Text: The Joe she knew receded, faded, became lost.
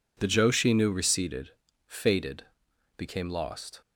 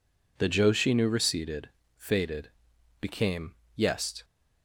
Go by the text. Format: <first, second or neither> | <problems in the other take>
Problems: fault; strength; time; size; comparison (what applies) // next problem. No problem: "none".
first | says "yest" for "lost"; at 3.7 s